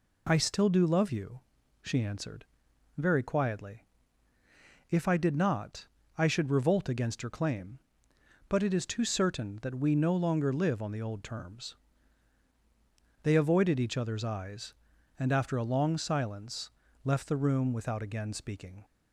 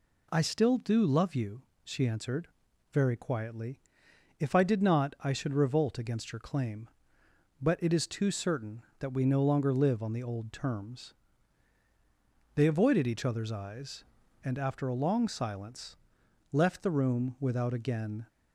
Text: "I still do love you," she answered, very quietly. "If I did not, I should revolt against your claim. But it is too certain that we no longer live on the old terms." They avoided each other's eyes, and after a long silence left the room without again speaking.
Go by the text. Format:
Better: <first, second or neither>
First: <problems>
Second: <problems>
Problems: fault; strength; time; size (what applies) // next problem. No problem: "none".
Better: first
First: pauses between "silence" and "left"; slight; at 16.6 s; 0.36 s long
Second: pauses between "silence" and "left"; noticeable; at 15.9 s; 0.56 s long // stops before "speaking"; at 18.2 s